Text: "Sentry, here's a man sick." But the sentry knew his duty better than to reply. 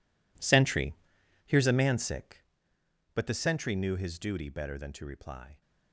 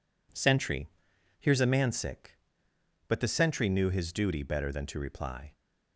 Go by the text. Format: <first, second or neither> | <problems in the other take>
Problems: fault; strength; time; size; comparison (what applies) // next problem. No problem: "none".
second | gets quieter; strong; throughout; 17 dB